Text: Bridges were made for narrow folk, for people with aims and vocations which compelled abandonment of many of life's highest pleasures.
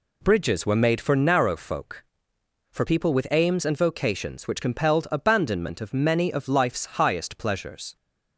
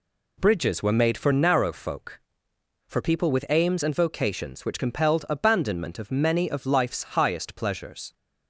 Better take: neither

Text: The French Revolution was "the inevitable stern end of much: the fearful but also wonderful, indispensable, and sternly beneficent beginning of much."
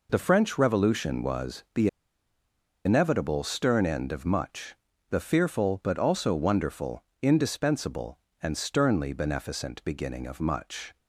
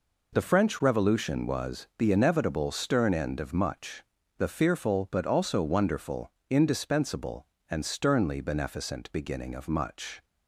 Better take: second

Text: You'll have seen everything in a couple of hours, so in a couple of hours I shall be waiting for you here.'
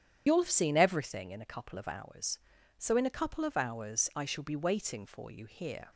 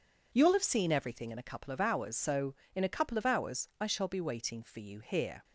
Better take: second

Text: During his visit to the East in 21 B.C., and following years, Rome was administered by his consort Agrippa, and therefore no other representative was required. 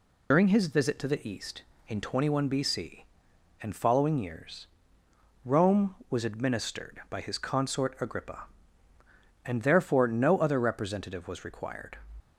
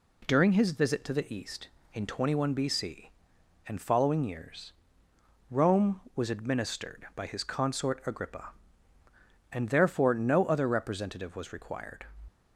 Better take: second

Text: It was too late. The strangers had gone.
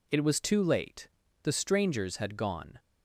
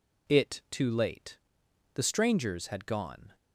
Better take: first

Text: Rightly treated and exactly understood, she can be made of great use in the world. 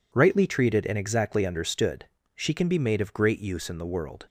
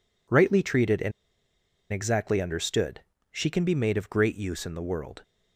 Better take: first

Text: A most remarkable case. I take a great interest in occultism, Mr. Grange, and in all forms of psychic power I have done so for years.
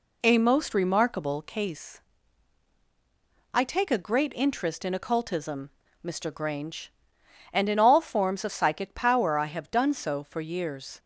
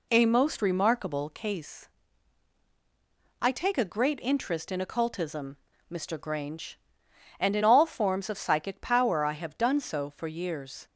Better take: neither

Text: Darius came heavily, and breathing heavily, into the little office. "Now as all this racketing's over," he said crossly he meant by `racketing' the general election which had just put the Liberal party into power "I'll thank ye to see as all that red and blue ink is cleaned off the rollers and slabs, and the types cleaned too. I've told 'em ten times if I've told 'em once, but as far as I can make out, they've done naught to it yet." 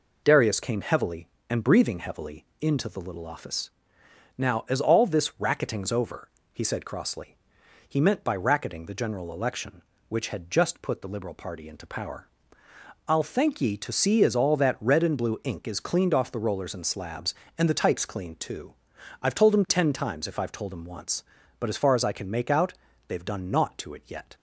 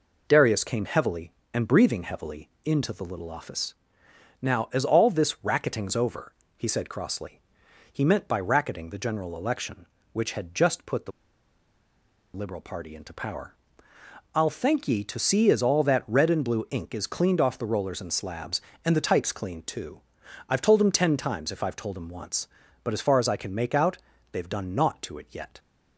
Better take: first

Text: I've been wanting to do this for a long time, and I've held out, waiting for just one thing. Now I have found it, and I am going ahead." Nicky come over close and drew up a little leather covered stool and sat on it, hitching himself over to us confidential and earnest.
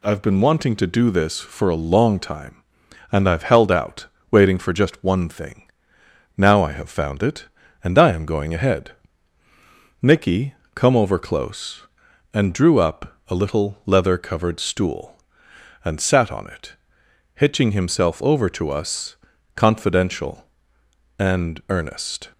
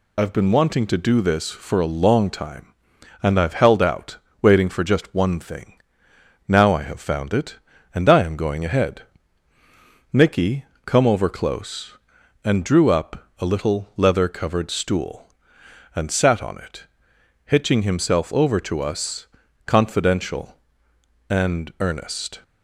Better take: first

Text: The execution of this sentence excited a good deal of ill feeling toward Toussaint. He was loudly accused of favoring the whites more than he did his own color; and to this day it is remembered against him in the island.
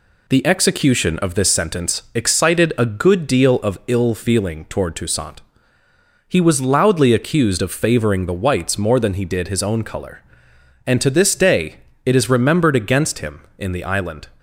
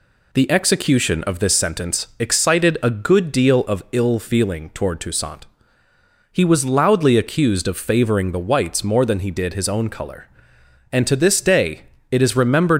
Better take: first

